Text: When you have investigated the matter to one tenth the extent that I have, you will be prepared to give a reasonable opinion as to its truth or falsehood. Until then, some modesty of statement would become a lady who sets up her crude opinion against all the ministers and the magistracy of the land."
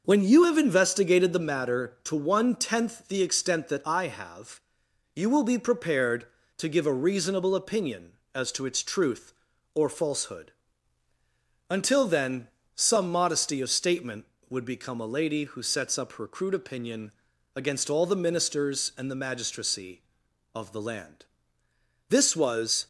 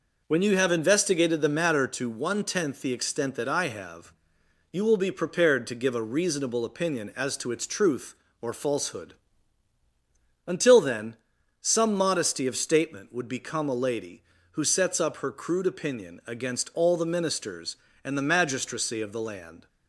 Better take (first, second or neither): second